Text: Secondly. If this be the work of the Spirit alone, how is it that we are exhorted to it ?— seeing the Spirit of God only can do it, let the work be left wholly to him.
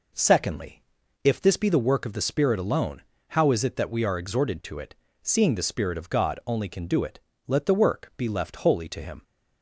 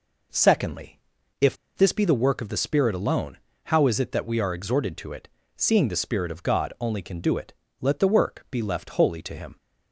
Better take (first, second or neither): first